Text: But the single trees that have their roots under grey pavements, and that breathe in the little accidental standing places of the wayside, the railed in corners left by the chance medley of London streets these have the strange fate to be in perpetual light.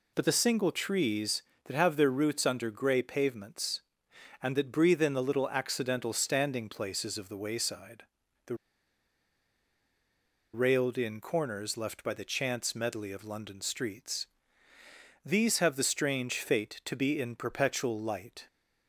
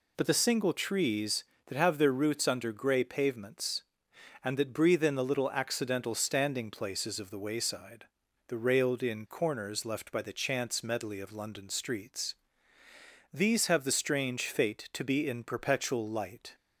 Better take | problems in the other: second | pauses between "the" and "railed"; strong; at 8.5 s; 1.9 s long // pauses between "streets" and "these"; noticeable; at 14.2 s; 0.96 s long; noticeable in the second

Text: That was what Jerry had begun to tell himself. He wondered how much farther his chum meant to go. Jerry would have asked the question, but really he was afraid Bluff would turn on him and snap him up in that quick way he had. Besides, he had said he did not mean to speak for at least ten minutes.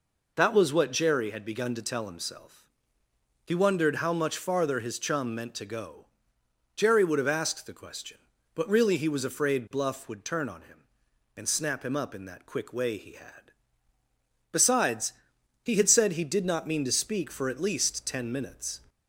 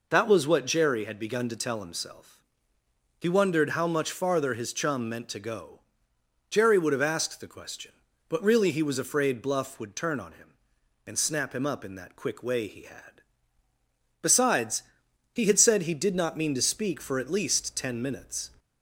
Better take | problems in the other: neither | none

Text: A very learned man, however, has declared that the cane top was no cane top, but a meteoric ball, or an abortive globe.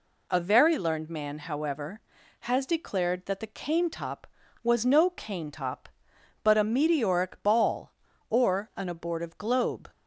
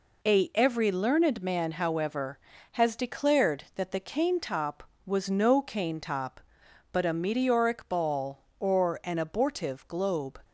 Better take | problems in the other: first | says "every" for "very"; at 0.5 s

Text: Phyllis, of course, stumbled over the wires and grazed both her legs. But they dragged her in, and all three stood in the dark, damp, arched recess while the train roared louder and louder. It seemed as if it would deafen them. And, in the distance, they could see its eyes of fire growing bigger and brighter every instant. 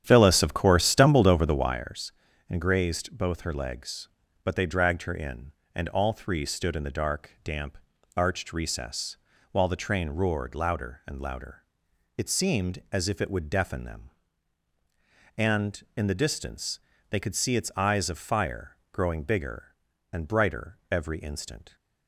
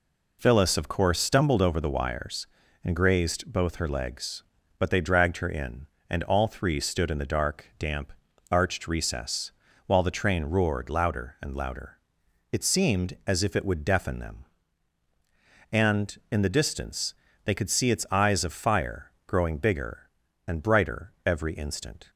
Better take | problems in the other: second | starts louder than the rest; strong; until 1.9 s; 10 dB // pauses between "recess" and "while"; slight; at 9.1 s; 0.34 s long; slight in the second

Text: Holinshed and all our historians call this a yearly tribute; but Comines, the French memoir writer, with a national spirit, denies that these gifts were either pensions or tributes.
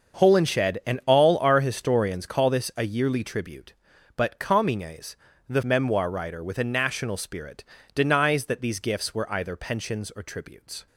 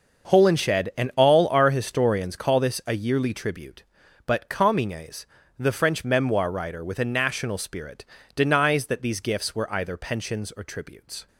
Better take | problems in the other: second | starts louder than the rest; until 1.3 s; 6.5 dB; also in the second // skips "French"; at 5.6 s

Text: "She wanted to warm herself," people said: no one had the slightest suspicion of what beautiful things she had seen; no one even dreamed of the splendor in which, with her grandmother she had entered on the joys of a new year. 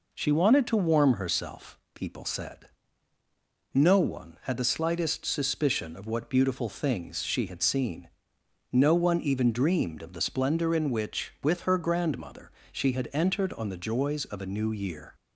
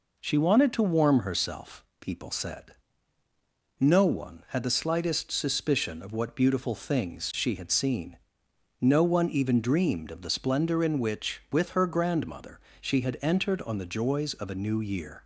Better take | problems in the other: neither | pauses between "grandmother" and "she"; slight; the same in both

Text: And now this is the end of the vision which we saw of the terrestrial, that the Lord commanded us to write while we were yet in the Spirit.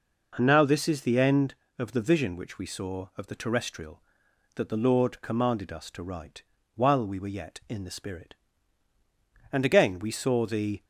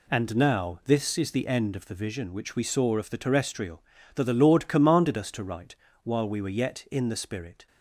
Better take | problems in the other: second | pauses between "write" and "while"; slight; at 6.4 s; 0.32 s long; slight in the second // goes on to say "And again we saw the"; from 9.5 s on; 1.3 s long

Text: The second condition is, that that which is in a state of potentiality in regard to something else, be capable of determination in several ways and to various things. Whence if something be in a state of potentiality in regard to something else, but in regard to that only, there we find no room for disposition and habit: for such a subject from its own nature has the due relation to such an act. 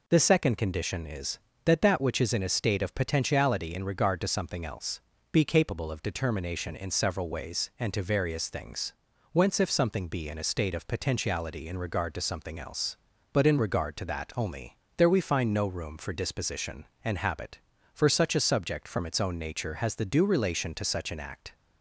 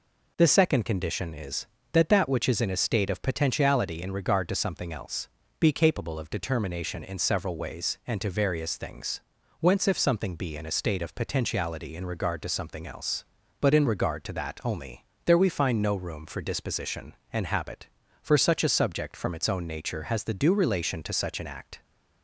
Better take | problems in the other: neither | none

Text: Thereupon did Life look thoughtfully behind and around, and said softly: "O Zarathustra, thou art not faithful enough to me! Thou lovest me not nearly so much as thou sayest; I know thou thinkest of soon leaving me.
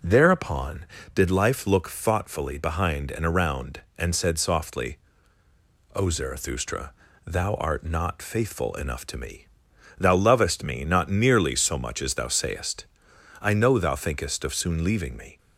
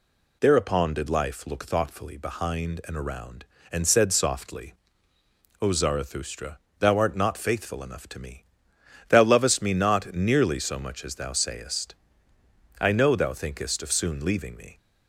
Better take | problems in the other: neither | none

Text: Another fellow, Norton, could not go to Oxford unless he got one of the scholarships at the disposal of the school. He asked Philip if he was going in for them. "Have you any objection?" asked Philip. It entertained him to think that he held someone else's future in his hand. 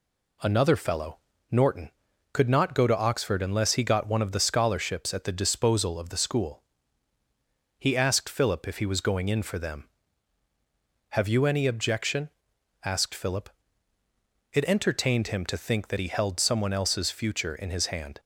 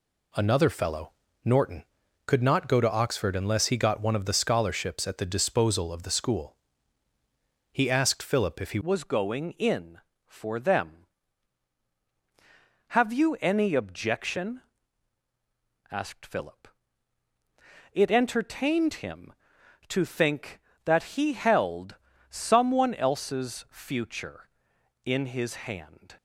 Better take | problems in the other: first | changes voice at "was"; from 8.8 s on; 17.3 s long // pauses between "held" and "someone"; slight; at 21.9 s; 0.34 s long

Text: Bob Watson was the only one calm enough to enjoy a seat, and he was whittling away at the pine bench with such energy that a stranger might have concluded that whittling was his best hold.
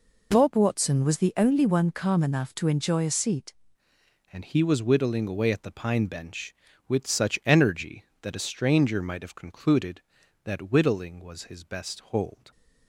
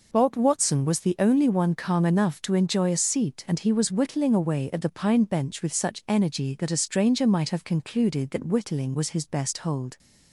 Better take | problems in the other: second | changes voice at "and"; from 4.3 s on; 8.2 s long

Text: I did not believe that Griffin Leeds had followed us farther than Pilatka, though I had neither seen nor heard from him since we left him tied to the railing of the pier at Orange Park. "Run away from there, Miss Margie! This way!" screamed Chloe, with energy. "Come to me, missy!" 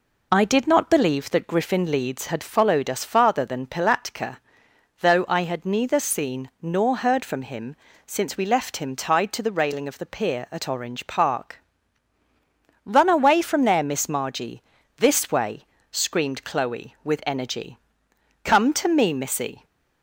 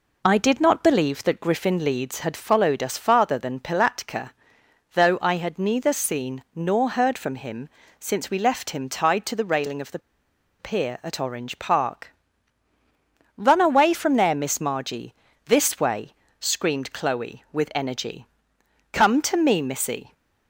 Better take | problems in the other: first | pauses between "him" and "since"; slight; at 7.6 s; 0.30 s long; slight in the first // pauses between "the" and "pier"; noticeable; at 9.9 s; 0.60 s long

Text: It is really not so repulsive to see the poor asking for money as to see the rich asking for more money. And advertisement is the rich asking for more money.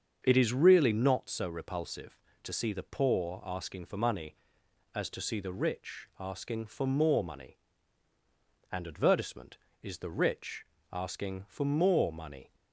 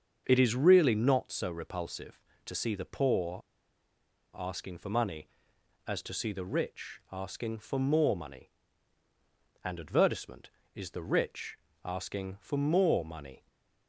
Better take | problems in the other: first | starts louder than the rest; until 1.2 s; 7 dB; also in the first // pauses between "poor" and "asking"; noticeable; at 3.4 s; 0.96 s long // pauses between "rich" and "asking"; slight; at 11.5 s; 0.26 s long; slight in the first // stays silent after the last word; slight; from 13.3 s on; 0.5 s long

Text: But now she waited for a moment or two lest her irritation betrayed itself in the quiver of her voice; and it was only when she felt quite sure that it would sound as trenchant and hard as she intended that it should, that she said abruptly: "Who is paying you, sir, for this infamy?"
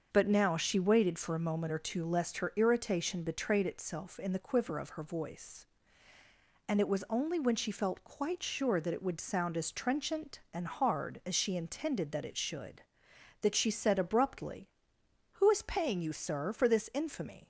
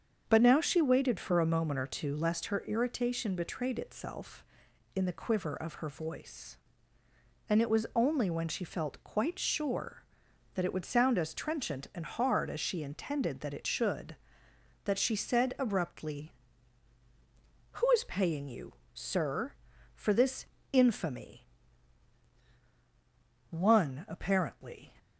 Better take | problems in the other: first | starts louder than the rest; until 1.2 s; 7 dB; also in the first // pauses between "this" and "infamy"; slight; at 20.4 s; 0.26 s long // goes on to say "One apparently"; from 23.5 s on; 1.4 s long

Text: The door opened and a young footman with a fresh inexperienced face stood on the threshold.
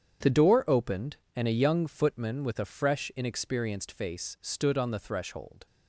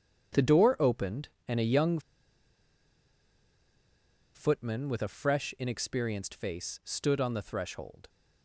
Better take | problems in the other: first | starts louder than the rest; strong; until 1.5 s; 8 dB; strong in the first // pauses between "young" and "footman"; strong; at 1.9 s; 2.3 s long

